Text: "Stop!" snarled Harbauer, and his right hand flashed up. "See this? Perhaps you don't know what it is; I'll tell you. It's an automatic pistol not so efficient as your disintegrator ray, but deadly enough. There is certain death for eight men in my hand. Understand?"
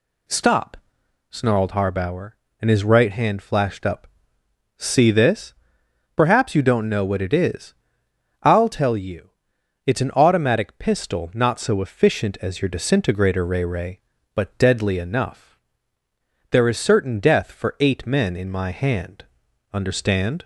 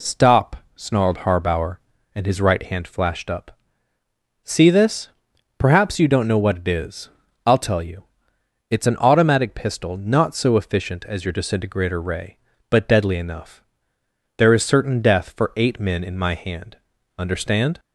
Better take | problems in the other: second | says "ray" twice; at 13.6 s

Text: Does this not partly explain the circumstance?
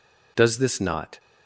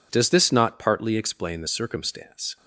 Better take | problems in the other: second | stops before "partly explain the circumstance"; at 1.1 s

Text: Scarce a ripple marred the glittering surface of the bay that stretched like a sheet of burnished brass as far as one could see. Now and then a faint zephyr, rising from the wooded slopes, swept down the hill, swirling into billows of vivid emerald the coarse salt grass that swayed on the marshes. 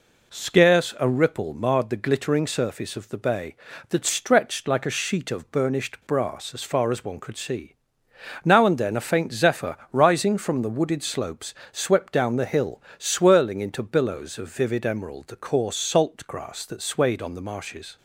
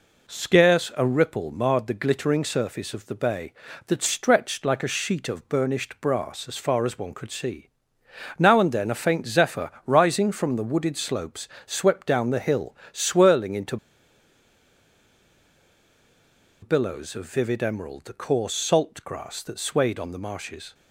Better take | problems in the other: first | pauses between "into" and "billows"; strong; at 13.7 s; 2.8 s long

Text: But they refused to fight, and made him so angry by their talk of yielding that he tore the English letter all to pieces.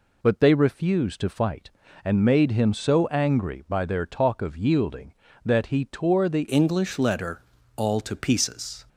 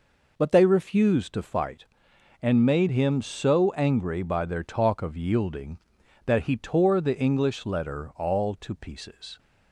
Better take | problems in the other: second | changes voice at "English"; from 6.4 s on; 2.4 s long // pauses between "letter" and "all"; slight; at 7.4 s; 0.34 s long

